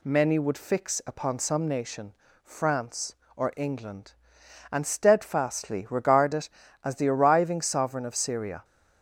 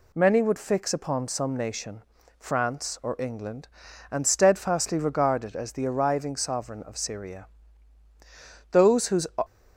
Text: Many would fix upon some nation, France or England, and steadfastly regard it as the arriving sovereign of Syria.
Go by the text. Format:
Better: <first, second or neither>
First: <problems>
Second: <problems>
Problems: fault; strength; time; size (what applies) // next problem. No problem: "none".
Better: first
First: none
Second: goes on to say "Those whose"; from 8.7 s on; 0.54 s long